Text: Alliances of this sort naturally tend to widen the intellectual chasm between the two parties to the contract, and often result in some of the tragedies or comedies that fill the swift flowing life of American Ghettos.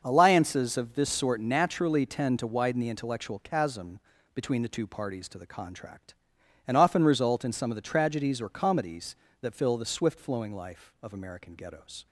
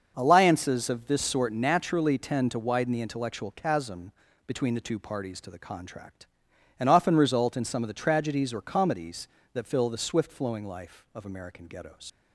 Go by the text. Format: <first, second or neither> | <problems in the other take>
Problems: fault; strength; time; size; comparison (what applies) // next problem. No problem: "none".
first | starts louder than the rest; noticeable; until 1.1 s; 6 dB; noticeable in the first // pauses between "chasm" and "between"; slight; at 4.1 s; 0.34 s long; slight in the first // leaves "Ghettos" unfinished; at 12.0 s; 85 ms